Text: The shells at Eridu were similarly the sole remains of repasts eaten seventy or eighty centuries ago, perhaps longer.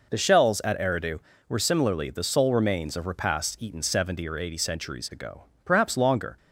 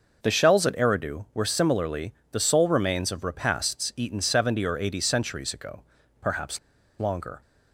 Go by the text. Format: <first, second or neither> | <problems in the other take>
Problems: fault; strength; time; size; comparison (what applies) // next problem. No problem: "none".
first | pauses between "similarly" and "the"; slight; at 2.1 s; 0.18 s long // pauses between "perhaps" and "longer"; at 6.5 s; 0.41 s long